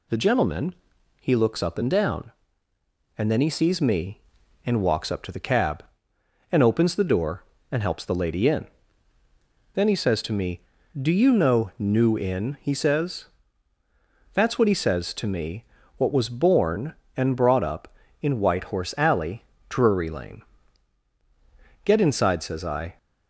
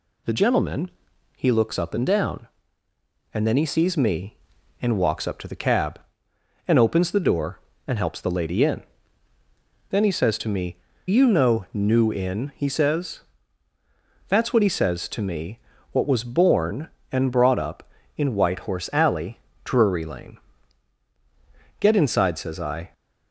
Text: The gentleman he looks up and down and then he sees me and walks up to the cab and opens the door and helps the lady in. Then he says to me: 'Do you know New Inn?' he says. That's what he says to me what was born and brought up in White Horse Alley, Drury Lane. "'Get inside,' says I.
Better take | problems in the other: first | pauses between "gentleman" and "he"; noticeable; at 0.8 s; 0.46 s long; noticeable in the first // skips "Do"; at 10.9 s // pauses between "me" and "what"; slight; at 15.5 s; 0.34 s long; slight in the first

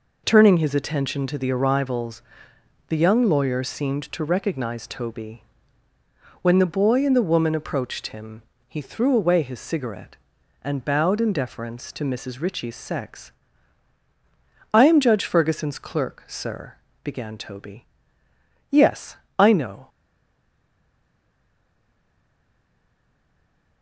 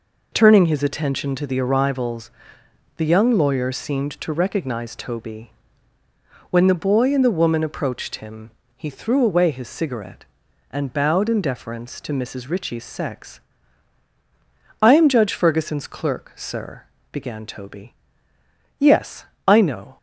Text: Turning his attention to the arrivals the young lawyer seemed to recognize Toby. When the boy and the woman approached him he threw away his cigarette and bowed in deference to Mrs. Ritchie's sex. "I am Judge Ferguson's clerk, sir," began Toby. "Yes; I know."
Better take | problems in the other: second | pauses between "arrivals" and "the"; noticeable; at 2.2 s; 0.66 s long; noticeable in the second // pauses between "him" and "he"; slight; at 8.4 s; 0.26 s long; slight in the second // stays silent after the last word; strong; from 19.8 s on; 4.0 s long

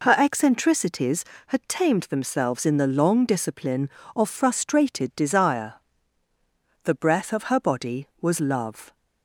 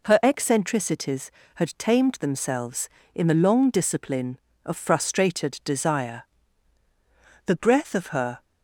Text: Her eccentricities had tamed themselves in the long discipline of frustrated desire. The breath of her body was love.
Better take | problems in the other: first | stops before "body was love"; at 8.4 s

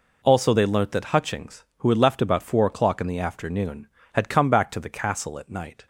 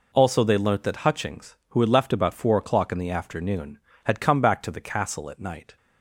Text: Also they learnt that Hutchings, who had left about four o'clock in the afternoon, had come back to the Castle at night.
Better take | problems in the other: neither | none

